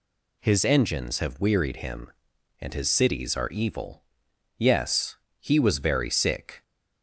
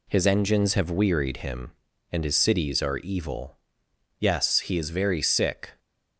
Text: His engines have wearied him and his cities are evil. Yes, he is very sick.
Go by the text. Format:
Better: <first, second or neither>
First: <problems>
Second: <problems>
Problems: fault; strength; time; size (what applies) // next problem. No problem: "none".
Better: second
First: says "was" for "is"; at 5.6 s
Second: none